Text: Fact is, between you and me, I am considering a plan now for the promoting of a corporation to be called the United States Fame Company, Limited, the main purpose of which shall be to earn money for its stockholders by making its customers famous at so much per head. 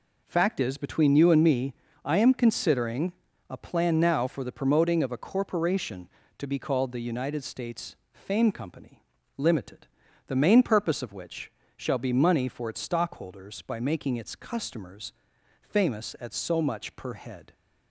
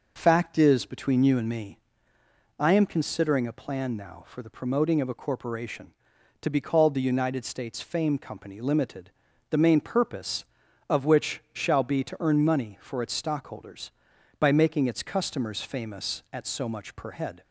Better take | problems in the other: second | pauses between "considering" and "a"; slight; at 3.1 s; 0.36 s long // pauses between "States" and "Fame"; slight; at 7.9 s; 0.18 s long // pauses between "which" and "shall"; slight; at 11.5 s; 0.26 s long // skips "to earn"; at 12.1 s // pauses between "customers" and "famous"; noticeable; at 15.1 s; 0.48 s long

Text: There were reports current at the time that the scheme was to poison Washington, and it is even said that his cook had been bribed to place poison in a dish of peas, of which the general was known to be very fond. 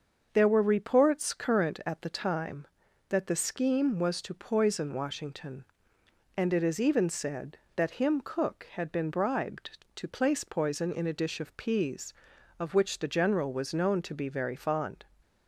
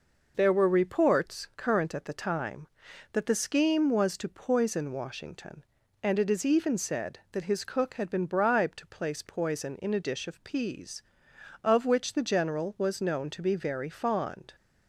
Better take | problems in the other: second | starts louder than the rest; until 1.3 s; 6.5 dB // says "him" for "his"; at 7.9 s

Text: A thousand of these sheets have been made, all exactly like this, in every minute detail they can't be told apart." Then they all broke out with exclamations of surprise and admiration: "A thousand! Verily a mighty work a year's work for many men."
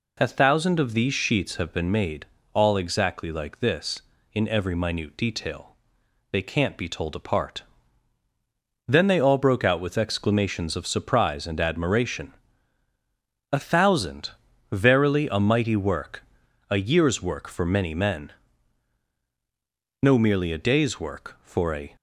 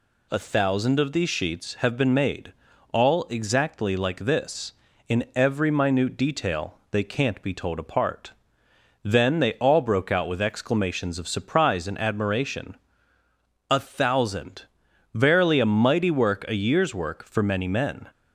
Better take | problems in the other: second | pauses between "detail" and "they"; noticeable; at 5.7 s; 0.56 s long // pauses between "work" and "a"; at 16.2 s; 0.44 s long // goes on to say "No merely a day's work for a"; strong; from 20.0 s on; 1.9 s long

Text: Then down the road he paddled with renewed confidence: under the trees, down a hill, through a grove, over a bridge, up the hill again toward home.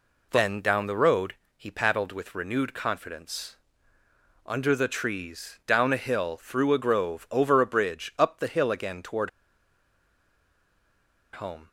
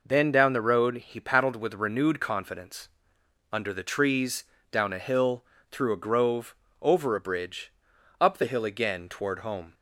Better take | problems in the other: second | pauses between "road" and "he"; slight; at 1.3 s; 0.22 s long // pauses between "toward" and "home"; strong; at 9.2 s; 2.0 s long

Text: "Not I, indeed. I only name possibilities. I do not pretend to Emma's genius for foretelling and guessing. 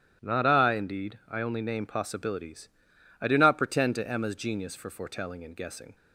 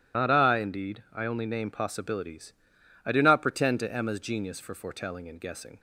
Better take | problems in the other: first | loses the start of "Not"; at 0.1 s; 95 ms // starts louder than the rest; strong; until 1.2 s; 12.5 dB; strong in the first

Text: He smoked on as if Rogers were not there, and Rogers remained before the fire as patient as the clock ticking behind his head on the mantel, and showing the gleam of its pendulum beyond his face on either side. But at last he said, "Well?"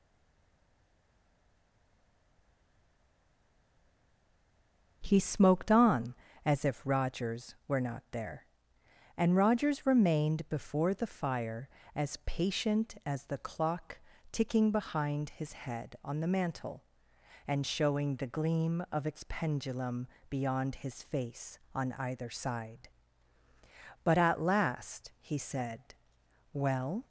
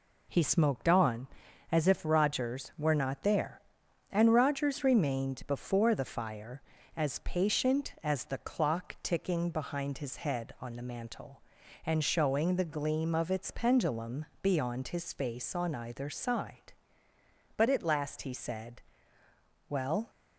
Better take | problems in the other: second | stays silent before the first word; strong; until 5.0 s; 5.0 s long // pauses between "clock" and "ticking"; slight; at 13.9 s; 0.32 s long // pauses between "pendulum" and "beyond"; slight; at 20.0 s; 0.24 s long; slight in the second

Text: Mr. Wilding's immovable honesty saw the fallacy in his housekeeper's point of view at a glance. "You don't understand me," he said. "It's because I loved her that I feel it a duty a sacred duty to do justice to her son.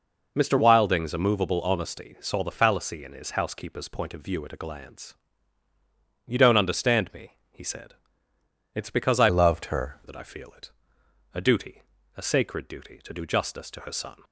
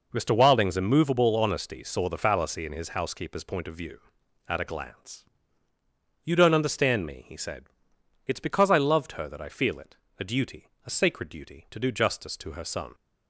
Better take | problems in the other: second | changes voice from "loved" to "her"; from 9.2 to 9.9 s; 0.7 s long // pauses between "it" and "a"; noticeable; at 10.6 s; 0.64 s long; slight in the second // pauses between "duty" and "a"; slight; at 11.8 s; 0.36 s long; slight in the second

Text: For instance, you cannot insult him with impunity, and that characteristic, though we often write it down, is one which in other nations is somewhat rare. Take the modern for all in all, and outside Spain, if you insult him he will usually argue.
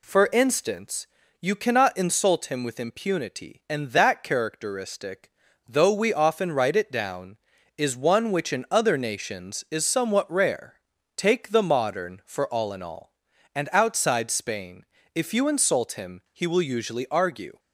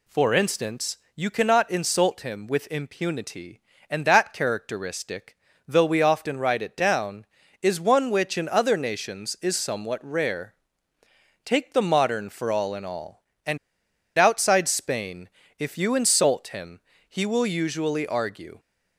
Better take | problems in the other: first | pauses between "and" and "outside"; noticeable; at 13.5 s; 0.59 s long // pauses between "him" and "he"; slight; at 16.7 s; 0.28 s long

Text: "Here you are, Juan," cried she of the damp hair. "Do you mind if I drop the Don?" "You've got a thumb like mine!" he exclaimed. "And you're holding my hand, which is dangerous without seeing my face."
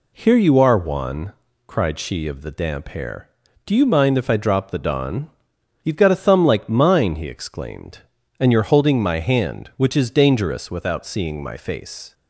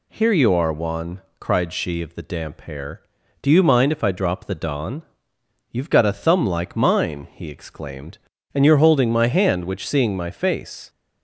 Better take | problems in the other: first | skips "is dangerous without"; at 9.8 s

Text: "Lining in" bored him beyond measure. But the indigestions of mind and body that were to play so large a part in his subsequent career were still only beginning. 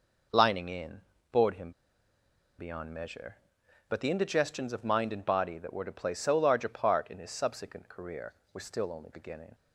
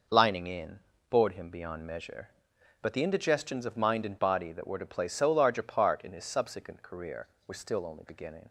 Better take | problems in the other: second | pauses between "in" and "bored"; slight; at 1.0 s; 0.30 s long; slight in the second // pauses between "him" and "beyond"; noticeable; at 1.7 s; 0.87 s long

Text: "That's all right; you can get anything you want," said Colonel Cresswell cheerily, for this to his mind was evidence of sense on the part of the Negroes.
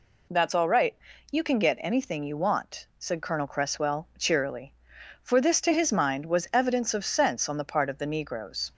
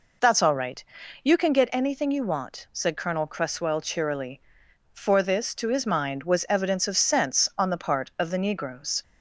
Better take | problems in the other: neither | none

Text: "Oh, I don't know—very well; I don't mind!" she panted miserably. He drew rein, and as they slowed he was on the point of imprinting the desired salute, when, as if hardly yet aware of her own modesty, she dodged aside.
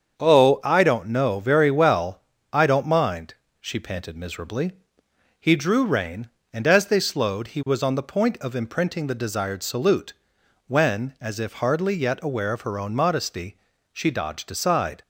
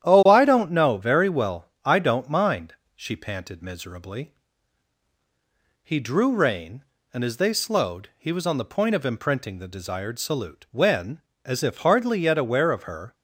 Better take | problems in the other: first | starts louder than the rest; strong; until 1.0 s; 10.5 dB; strong in the first // stops before "own modesty she dodged aside"; at 13.1 s

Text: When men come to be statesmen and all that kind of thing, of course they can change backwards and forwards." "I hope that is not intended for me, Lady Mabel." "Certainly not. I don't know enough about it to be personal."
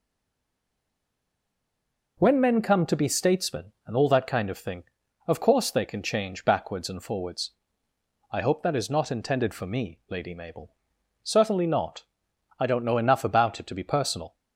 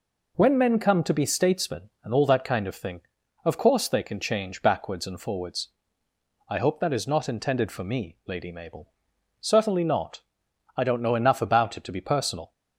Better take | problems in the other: second | stays silent before the first word; until 2.1 s; 2.1 s long

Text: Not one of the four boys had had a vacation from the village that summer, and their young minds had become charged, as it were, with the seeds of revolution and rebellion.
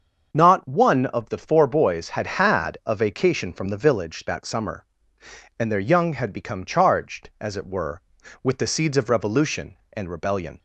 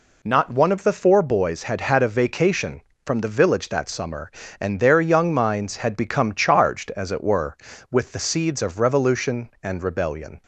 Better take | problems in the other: second | starts louder than the rest; until 1.3 s; 6.5 dB // skips "minds"; at 6.1 s

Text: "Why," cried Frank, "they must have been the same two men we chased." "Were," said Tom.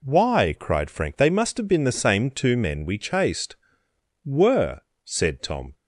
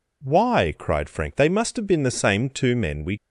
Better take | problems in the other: first | stops before "chased Were said Tom"; at 3.1 s

